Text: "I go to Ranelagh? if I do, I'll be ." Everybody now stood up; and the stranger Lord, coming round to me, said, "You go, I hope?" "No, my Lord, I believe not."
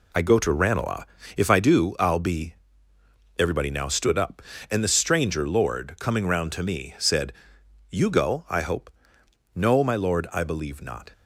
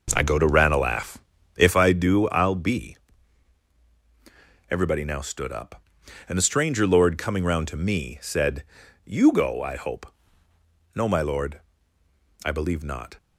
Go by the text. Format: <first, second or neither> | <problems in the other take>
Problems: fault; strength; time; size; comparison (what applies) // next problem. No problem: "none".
first | starts louder than the rest; noticeable; until 1.9 s; 5.5 dB